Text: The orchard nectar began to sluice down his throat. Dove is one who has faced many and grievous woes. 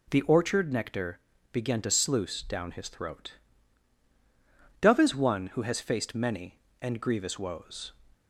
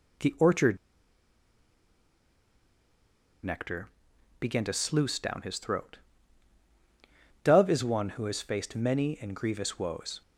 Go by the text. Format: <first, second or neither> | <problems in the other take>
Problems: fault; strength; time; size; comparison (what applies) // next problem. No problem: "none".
first | pauses between "orchard" and "nectar"; strong; at 0.7 s; 2.6 s long // pauses between "nectar" and "began"; noticeable; at 3.8 s; 0.50 s long; slight in the first